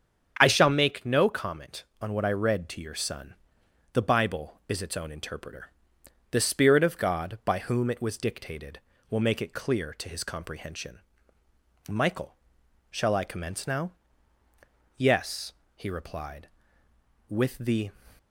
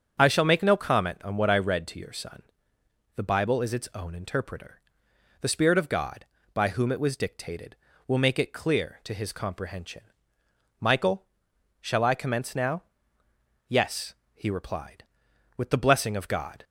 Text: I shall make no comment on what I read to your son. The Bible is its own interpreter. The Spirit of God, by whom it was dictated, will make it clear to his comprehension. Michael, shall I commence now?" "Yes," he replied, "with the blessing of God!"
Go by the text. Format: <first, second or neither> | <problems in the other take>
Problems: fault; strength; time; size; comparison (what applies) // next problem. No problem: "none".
second | starts louder than the rest; strong; until 1.4 s; 8 dB; also in the second // stops before "blessing of God"; at 18.1 s